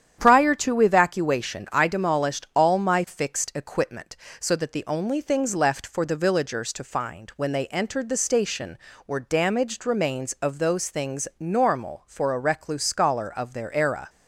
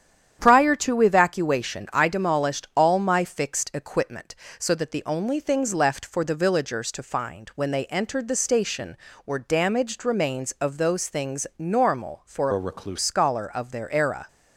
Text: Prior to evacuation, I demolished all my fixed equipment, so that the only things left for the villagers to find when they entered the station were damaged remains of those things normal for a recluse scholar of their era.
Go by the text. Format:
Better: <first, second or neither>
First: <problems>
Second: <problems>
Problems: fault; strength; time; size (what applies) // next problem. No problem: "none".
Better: first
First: starts louder than the rest; strong; until 1.2 s; 9.5 dB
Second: starts louder than the rest; strong; until 1.4 s; 9.5 dB // changes voice from "a" to "recluse"; from 12.5 to 12.9 s; 0.4 s long